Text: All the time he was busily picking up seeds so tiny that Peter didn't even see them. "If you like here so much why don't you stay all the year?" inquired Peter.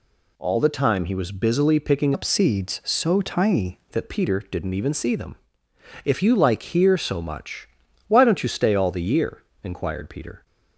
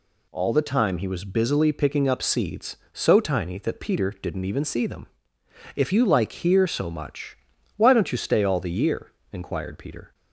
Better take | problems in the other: second | changes voice from "up" to "tiny"; from 2.1 to 3.7 s; 1.6 s long // pauses between "much" and "why"; at 7.6 s; 0.38 s long; also in the second

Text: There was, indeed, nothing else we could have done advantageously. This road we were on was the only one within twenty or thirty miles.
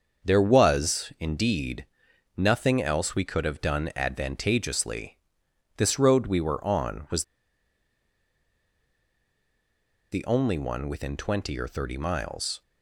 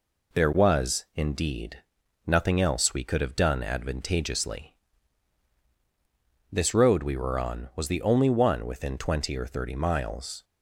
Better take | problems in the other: second | starts louder than the rest; until 1.3 s; 6.5 dB // pauses between "was" and "the"; strong; at 7.2 s; 2.8 s long

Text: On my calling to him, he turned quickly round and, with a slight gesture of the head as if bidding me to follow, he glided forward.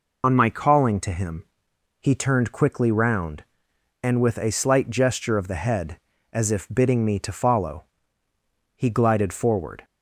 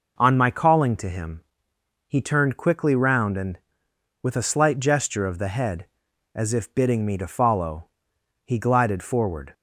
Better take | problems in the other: second | loses the start of "On"; at 0.2 s; 35 ms

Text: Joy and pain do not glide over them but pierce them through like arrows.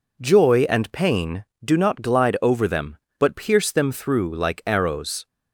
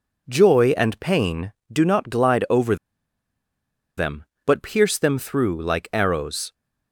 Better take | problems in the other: first | pauses between "over" and "them"; at 2.7 s; 1.2 s long

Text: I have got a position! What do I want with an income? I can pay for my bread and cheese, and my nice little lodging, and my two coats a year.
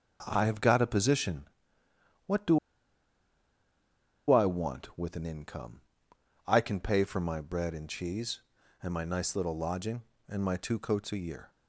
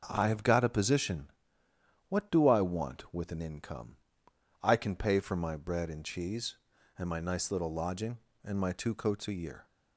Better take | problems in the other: second | starts louder than the rest; noticeable; until 1.2 s; 6 dB; noticeable in the second // pauses between "do" and "I"; strong; at 2.5 s; 1.7 s long

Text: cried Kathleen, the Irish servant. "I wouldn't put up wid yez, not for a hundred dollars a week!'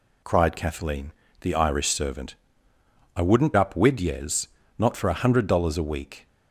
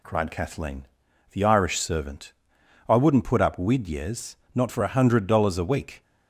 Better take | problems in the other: second | skips "put"; at 3.5 s

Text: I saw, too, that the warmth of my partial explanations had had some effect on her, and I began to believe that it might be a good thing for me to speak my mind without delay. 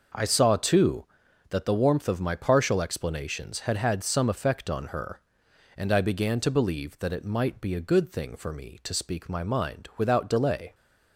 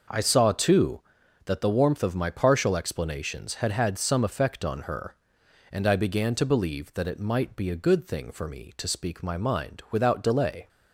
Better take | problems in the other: neither | none

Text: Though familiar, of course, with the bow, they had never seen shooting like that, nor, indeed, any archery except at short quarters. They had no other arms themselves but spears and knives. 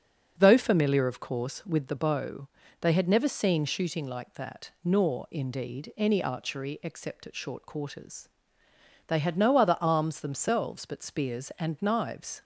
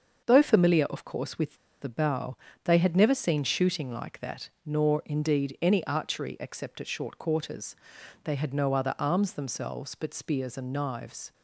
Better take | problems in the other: first | starts louder than the rest; until 1.2 s; 6.5 dB; also in the first // pauses between "with" and "the"; slight; at 1.5 s; 0.24 s long

